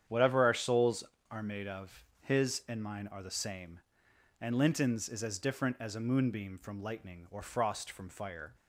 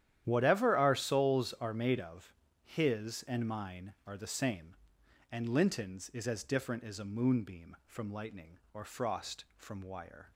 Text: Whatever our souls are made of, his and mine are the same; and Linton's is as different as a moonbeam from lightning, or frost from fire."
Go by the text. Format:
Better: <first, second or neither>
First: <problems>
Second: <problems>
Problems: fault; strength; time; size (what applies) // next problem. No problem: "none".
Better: first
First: starts louder than the rest; strong; until 1.3 s; 9 dB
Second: starts louder than the rest; strong; until 1.2 s; 11 dB // says "wire" for "fire"; at 9.8 s